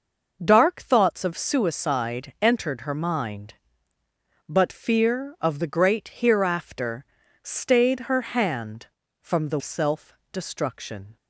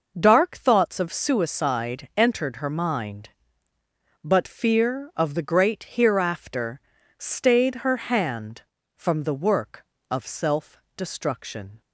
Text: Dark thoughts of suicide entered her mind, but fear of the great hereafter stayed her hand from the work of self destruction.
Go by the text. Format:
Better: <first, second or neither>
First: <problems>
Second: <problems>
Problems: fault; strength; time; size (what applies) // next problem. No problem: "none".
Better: second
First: pauses between "hereafter" and "stayed"; at 7.0 s; 0.38 s long // skips "work of"; at 9.6 s // pauses between "self" and "destruction"; slight; at 10.1 s; 0.20 s long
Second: pauses between "hereafter" and "stayed"; at 6.7 s; 0.38 s long // pauses between "self" and "destruction"; slight; at 10.7 s; 0.20 s long